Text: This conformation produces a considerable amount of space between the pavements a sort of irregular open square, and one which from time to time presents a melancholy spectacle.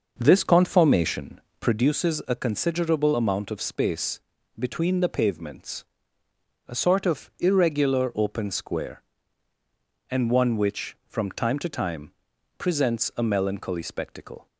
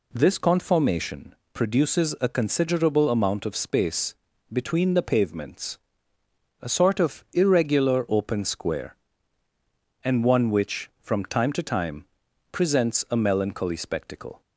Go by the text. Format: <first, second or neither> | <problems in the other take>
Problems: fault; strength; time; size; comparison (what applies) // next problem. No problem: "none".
second | starts louder than the rest; noticeable; until 1.9 s; 6 dB // pauses between "conformation" and "produces"; slight; at 1.3 s; 0.20 s long; slight in the second // pauses between "space" and "between"; slight; at 4.2 s; 0.36 s long; slight in the second // pauses between "pavements" and "a"; noticeable; at 5.8 s; 0.84 s long; noticeable in the second // pauses between "time" and "presents"; noticeable; at 12.1 s; 0.46 s long; noticeable in the second